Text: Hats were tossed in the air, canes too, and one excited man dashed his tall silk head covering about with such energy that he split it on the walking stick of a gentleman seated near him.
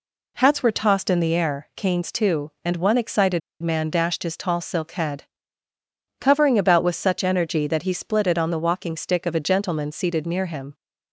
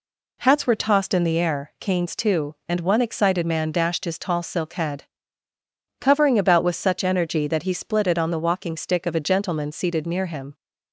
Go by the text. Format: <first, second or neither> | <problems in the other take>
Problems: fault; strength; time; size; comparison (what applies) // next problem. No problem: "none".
second | pauses between "excited" and "man"; slight; at 3.4 s; 0.22 s long // pauses between "head" and "covering"; noticeable; at 5.2 s; 0.96 s long; noticeable in the second